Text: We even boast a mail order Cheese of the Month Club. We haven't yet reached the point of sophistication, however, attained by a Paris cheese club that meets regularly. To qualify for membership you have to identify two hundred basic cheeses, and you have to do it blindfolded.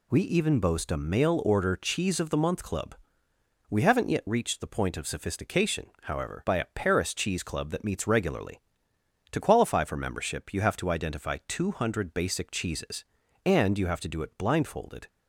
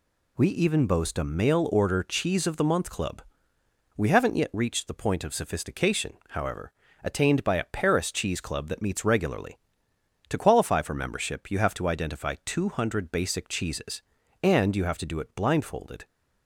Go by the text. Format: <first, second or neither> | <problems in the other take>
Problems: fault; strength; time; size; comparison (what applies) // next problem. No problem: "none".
second | skips "attained"; at 6.4 s